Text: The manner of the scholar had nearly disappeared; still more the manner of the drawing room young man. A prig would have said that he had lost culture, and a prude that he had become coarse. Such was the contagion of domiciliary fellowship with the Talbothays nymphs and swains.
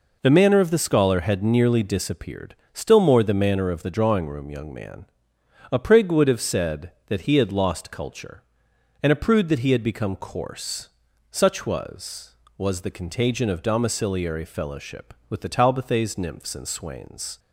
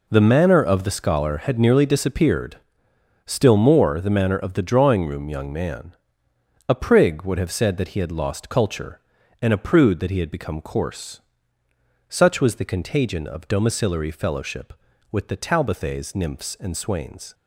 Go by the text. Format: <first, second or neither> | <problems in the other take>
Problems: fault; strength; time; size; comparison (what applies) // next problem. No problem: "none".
second | says "was" twice; at 12.5 s